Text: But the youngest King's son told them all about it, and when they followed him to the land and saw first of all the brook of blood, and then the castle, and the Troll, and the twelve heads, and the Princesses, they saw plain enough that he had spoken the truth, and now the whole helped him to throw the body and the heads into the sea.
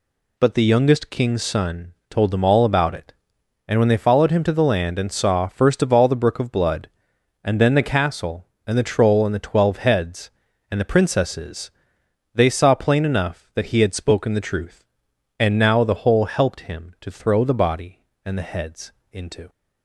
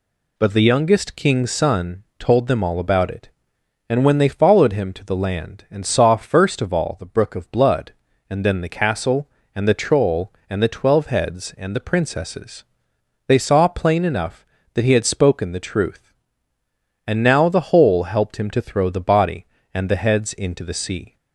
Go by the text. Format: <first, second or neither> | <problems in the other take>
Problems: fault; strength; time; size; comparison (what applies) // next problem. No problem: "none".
second | pauses between "son" and "told"; slight; at 1.9 s; 0.16 s long; slight in the second // pauses between "heads" and "into"; slight; at 18.9 s; 0.20 s long // stops before "the sea"; at 19.4 s